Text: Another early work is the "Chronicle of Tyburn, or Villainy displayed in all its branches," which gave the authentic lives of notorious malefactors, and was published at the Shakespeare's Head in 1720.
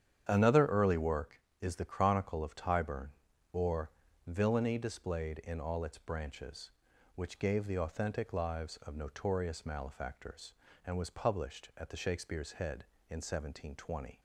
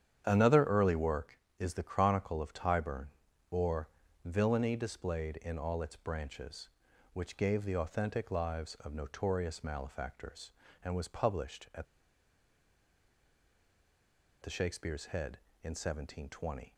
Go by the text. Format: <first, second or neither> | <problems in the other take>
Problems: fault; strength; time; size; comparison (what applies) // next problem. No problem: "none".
first | starts louder than the rest; strong; until 1.2 s; 9 dB; strong in the first // pauses between "or" and "Villainy"; slight; at 3.8 s; 0.36 s long; slight in the first // pauses between "at" and "the"; strong; at 11.8 s; 2.5 s long